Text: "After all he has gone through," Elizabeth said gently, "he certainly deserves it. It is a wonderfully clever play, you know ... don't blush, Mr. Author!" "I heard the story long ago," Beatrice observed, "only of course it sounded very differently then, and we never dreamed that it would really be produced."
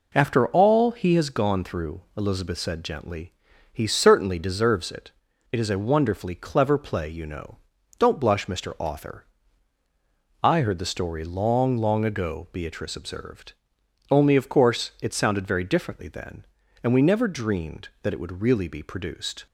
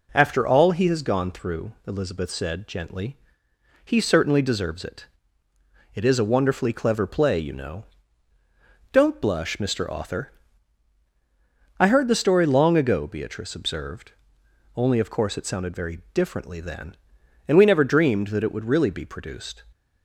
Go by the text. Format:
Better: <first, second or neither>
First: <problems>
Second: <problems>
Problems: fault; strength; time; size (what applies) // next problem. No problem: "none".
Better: second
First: says "long" twice; at 11.7 s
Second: none